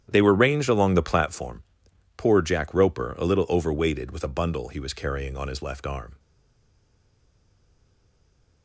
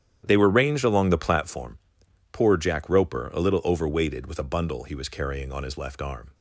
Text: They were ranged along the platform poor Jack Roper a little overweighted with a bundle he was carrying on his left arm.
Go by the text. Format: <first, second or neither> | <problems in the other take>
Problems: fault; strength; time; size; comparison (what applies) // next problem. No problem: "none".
second | starts louder than the rest; strong; until 1.1 s; 10 dB; strong in the second // pauses between "platform" and "poor"; noticeable; at 1.6 s; 0.54 s long; noticeable in the second // stays silent after the last word; from 6.1 s on; 2.5 s long